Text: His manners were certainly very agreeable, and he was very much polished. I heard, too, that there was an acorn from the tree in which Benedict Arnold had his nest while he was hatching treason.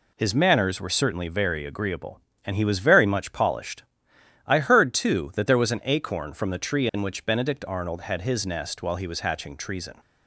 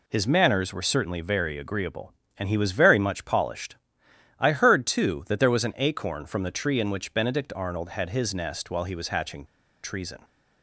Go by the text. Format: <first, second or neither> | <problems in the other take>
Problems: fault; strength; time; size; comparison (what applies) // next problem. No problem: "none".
first | pauses between "hatching" and "treason"; at 9.4 s; 0.39 s long